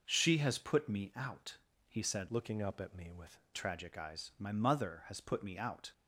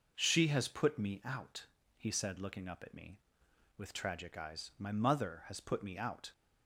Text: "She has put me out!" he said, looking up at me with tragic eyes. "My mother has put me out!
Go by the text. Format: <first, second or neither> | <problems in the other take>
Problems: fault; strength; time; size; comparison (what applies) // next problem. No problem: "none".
second | changes voice from "looking" to "with"; from 2.2 to 3.3 s; 1.1 s long